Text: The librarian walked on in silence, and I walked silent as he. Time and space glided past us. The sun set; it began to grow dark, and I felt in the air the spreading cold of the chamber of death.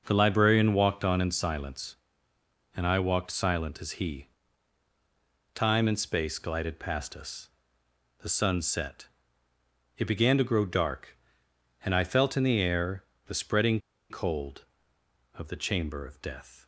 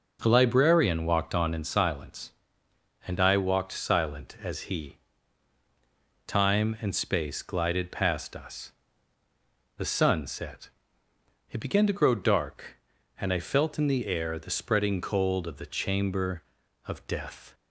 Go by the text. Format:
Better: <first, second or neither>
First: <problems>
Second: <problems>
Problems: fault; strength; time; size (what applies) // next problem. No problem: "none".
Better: second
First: pauses between "air" and "the"; slight; at 13.0 s; 0.24 s long // pauses between "spreading" and "cold"; slight; at 13.8 s; 0.29 s long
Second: none